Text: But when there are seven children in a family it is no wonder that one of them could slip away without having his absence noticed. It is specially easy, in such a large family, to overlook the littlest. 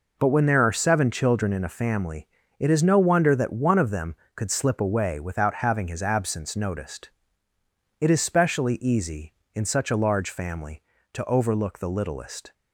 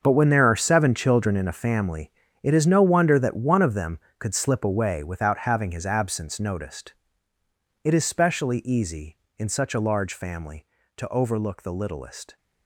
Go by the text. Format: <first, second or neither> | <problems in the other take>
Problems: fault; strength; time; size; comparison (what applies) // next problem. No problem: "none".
first | gets quieter; strong; throughout; 13.5 dB // pauses between "family" and "it"; slight; at 2.1 s; 0.30 s long; slight in the first